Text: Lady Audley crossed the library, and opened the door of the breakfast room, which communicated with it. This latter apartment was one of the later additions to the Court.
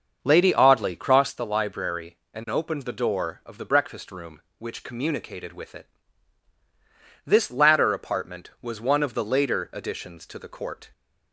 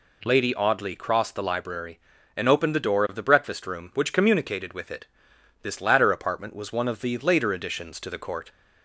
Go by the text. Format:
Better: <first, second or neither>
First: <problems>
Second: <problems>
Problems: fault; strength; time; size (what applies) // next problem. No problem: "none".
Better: second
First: starts louder than the rest; until 1.3 s; 6.5 dB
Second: none